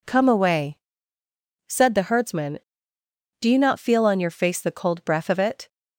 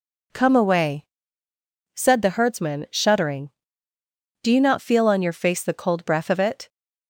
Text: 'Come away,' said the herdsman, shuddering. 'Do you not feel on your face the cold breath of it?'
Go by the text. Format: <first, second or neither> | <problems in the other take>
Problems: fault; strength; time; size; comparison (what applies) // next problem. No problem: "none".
second | skips "shuddering"; at 2.9 s